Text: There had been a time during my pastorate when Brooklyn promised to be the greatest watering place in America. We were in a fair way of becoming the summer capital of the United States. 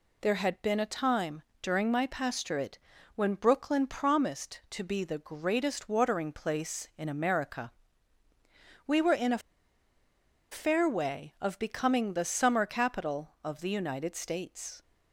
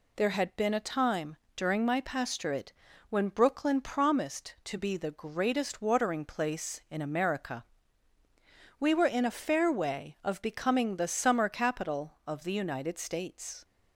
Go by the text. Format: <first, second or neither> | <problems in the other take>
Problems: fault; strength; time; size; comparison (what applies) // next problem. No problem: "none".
second | pauses between "time" and "during"; slight; at 1.4 s; 0.18 s long; slight in the second // pauses between "pastorate" and "when"; slight; at 2.7 s; 0.34 s long; slight in the second // pauses between "a" and "fair"; at 9.4 s; 1.1 s long